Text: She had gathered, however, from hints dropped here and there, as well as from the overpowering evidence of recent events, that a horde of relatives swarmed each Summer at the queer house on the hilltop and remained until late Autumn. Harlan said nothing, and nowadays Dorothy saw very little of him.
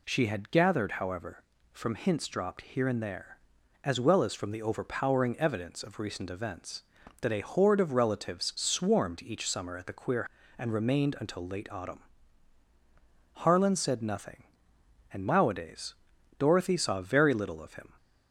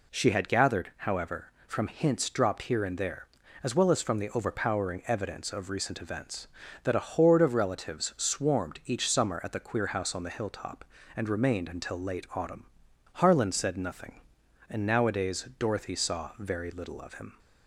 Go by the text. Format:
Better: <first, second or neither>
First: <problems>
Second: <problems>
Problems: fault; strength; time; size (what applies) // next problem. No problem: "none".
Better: second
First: skips "house on the hilltop"; at 10.4 s // pauses between "nowadays" and "Dorothy"; at 15.9 s; 0.42 s long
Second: none